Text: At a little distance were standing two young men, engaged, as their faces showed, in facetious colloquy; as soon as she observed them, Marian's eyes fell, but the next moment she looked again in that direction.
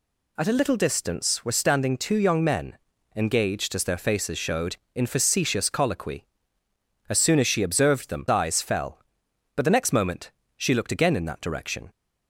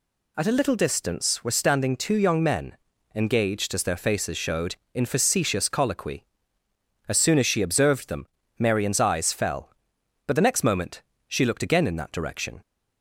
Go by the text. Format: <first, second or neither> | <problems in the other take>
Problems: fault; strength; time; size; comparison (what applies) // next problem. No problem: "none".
second | skips "Marian's"; at 8.2 s // pauses between "moment" and "she"; slight; at 10.3 s; 0.24 s long; slight in the second